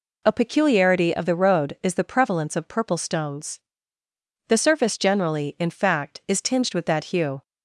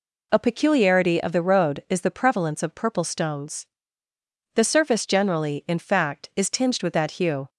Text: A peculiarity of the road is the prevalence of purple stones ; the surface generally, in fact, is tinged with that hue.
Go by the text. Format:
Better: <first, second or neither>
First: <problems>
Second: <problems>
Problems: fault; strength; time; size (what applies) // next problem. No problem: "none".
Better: neither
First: none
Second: none